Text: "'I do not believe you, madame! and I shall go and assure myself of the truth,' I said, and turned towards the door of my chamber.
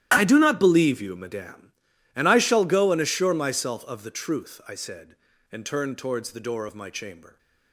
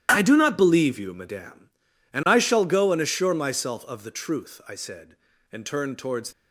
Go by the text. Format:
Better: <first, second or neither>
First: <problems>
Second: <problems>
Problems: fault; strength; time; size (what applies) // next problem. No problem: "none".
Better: first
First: starts louder than the rest; strong; until 1.1 s; 12 dB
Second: starts louder than the rest; strong; until 1.1 s; 11.5 dB // stops before "the door of my chamber"; at 6.3 s